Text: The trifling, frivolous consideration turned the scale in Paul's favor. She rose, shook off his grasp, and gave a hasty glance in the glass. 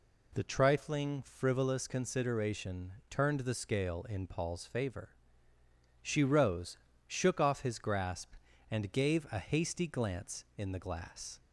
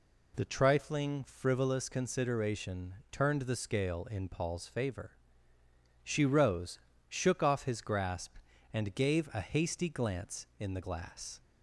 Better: neither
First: none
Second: none

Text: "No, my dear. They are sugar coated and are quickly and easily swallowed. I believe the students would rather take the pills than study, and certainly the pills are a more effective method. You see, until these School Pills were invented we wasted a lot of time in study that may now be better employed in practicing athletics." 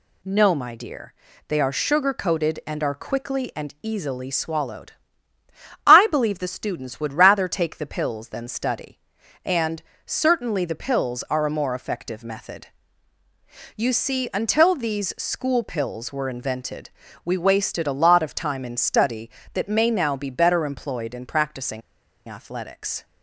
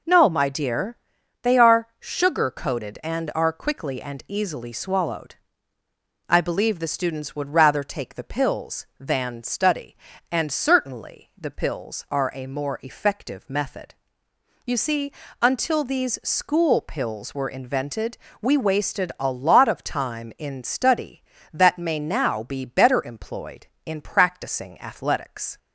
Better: second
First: pauses between "and" and "certainly"; slight; at 9.8 s; 0.24 s long // pauses between "invented" and "we"; slight; at 16.8 s; 0.34 s long // pauses between "practicing" and "athletics"; noticeable; at 21.8 s; 0.48 s long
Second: pauses between "invented" and "we"; slight; at 18.1 s; 0.24 s long

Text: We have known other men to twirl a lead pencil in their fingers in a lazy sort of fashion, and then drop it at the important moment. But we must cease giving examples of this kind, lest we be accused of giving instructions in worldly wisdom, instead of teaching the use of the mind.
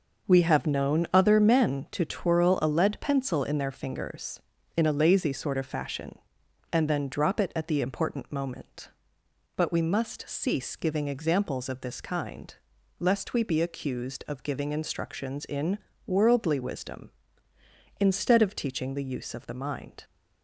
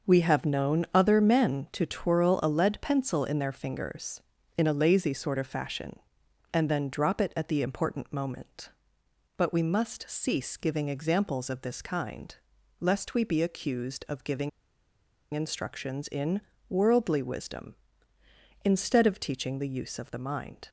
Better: first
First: pauses between "in" and "worldly"; slight; at 15.7 s; 0.28 s long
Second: pauses between "giving" and "instructions"; noticeable; at 14.4 s; 0.83 s long // pauses between "in" and "worldly"; slight; at 16.4 s; 0.28 s long

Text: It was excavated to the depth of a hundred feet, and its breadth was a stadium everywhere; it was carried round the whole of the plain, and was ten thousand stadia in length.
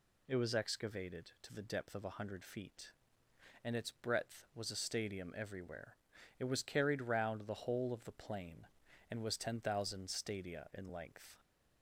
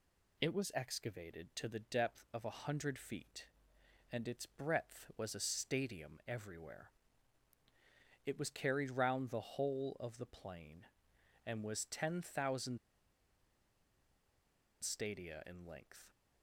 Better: first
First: none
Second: pauses between "thousand" and "stadia"; strong; at 12.7 s; 2.0 s long

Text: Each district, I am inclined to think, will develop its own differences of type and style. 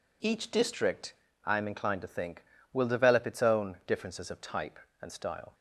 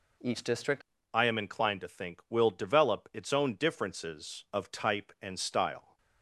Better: first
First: none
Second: changes voice at "I"; from 1.1 s on; 4.8 s long

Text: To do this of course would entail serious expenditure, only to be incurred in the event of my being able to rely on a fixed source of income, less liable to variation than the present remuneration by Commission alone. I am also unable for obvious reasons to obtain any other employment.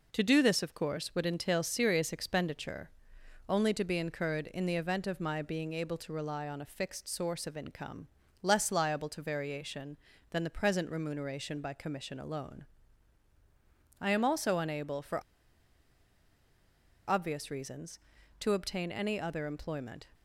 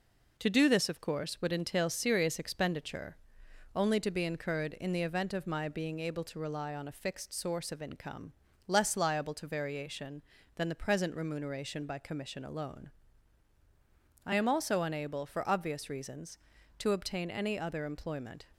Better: second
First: pauses between "for" and "obvious"; strong; at 15.2 s; 1.8 s long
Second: none

